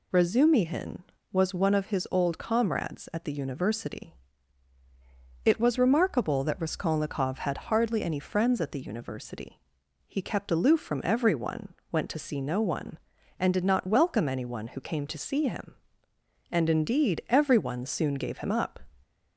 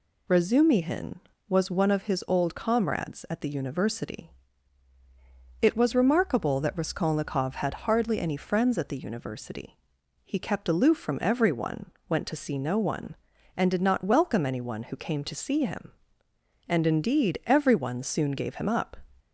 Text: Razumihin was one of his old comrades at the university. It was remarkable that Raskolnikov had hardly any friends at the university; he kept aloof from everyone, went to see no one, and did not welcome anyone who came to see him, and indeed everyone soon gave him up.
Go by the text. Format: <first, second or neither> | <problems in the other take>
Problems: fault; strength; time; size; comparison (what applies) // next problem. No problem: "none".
neither | none